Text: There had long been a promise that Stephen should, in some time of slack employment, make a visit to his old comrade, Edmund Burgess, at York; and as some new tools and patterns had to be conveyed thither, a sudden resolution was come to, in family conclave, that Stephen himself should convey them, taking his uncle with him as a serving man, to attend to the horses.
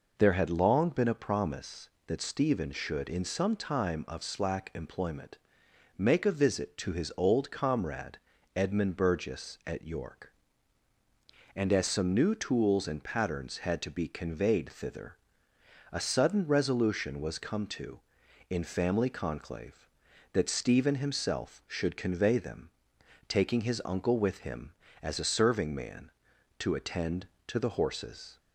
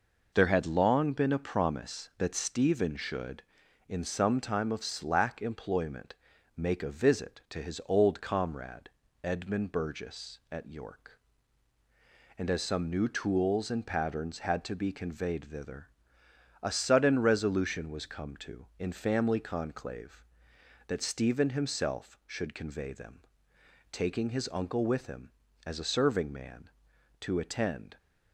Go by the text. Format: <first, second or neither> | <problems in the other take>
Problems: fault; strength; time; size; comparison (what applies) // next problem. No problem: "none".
first | stops before "to the horses"; at 27.9 s